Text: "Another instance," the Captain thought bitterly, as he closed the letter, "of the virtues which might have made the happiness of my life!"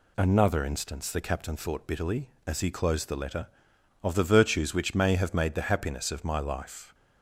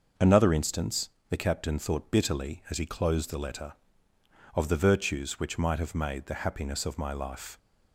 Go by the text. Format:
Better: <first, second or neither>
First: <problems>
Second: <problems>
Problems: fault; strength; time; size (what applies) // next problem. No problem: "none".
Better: second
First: says "may" for "might"; at 4.9 s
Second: none